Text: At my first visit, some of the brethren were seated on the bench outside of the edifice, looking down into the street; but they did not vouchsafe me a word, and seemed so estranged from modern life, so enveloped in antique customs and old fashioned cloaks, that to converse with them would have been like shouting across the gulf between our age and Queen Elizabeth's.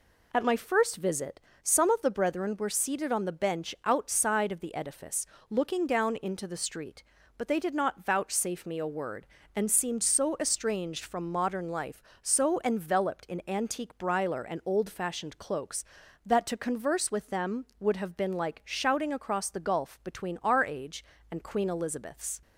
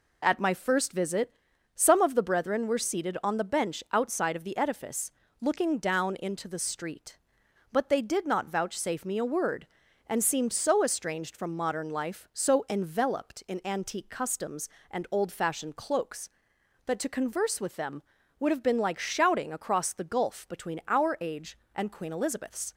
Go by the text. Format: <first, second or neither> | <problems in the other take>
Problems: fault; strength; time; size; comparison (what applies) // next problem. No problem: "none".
second | says "briler" for "customs"; at 13.9 s